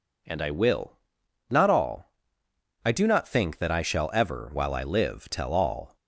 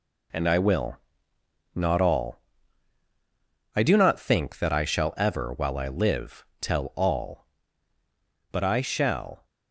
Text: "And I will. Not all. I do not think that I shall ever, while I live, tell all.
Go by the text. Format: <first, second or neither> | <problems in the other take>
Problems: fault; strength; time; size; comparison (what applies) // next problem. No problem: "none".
first | goes on to say "But I shall"; noticeable; from 8.5 s on; 0.94 s long